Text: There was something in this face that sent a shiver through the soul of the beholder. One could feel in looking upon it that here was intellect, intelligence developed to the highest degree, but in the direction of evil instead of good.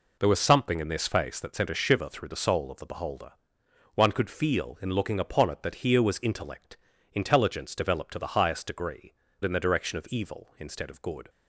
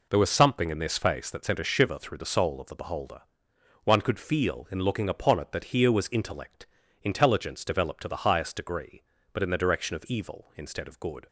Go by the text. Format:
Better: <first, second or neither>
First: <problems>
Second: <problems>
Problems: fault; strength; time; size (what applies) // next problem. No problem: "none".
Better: second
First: skips "but"; at 9.2 s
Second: none